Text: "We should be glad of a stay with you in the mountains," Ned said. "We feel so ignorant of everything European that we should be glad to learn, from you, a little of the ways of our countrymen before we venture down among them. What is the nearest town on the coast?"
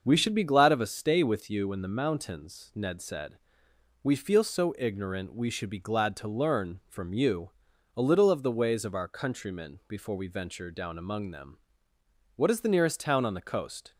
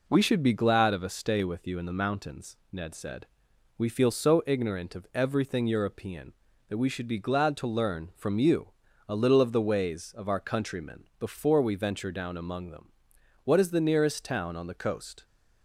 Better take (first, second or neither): second